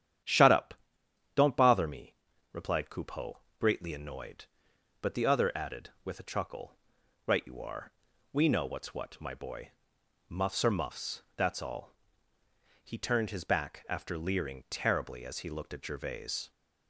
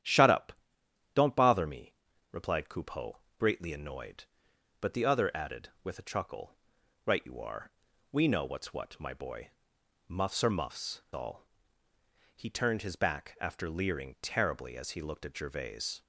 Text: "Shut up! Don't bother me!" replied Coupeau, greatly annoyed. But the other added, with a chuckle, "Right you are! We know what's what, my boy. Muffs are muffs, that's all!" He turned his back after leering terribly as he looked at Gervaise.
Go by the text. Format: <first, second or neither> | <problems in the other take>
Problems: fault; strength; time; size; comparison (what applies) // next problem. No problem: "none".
first | starts louder than the rest; strong; until 1.6 s; 10.5 dB; strong in the first // skips "that's"; at 11.0 s